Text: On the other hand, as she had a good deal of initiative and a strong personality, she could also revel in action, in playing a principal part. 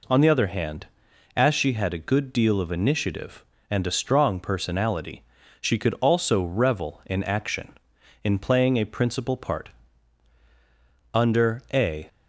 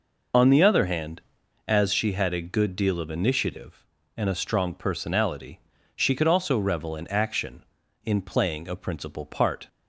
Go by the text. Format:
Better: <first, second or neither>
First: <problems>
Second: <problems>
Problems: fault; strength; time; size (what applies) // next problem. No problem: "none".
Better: second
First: goes on to say "Under a"; noticeable; from 11.1 s on; 0.94 s long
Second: none